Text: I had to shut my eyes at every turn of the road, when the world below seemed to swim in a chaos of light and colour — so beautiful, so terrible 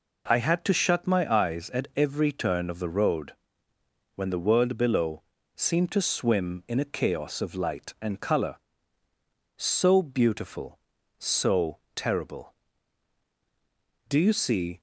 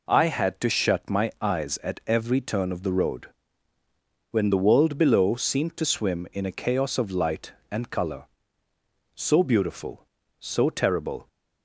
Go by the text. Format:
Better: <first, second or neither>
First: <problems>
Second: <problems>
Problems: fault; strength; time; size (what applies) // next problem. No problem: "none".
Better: second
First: pauses between "below" and "seemed"; slight; at 5.2 s; 0.32 s long // pauses between "so" and "terrible"; slight; at 11.7 s; 0.18 s long // goes on to say "Do you see"; noticeable; from 14.0 s on; 0.70 s long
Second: none